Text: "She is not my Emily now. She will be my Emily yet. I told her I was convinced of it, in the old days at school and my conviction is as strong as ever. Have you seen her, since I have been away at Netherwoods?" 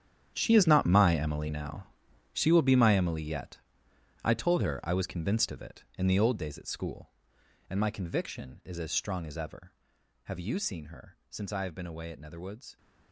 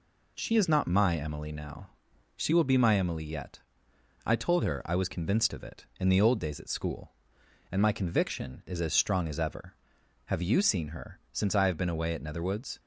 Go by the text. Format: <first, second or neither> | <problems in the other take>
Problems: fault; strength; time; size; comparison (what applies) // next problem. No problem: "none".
second | gets quieter; strong; throughout; 15 dB